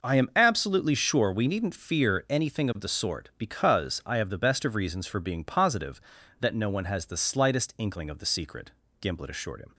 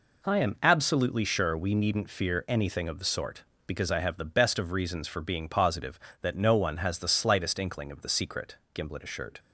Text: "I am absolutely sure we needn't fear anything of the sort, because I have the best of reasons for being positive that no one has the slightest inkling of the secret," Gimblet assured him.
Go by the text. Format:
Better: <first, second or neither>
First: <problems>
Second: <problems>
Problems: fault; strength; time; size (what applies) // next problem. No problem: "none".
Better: first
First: none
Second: stops before "him"; at 9.3 s